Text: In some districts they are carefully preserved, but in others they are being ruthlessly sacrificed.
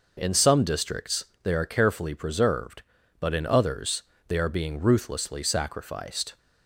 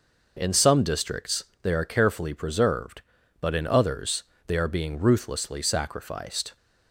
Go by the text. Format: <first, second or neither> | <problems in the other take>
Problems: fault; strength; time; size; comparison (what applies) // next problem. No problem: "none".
neither | pauses between "districts" and "they"; slight; the same in both // pauses between "others" and "they"; slight; the same in both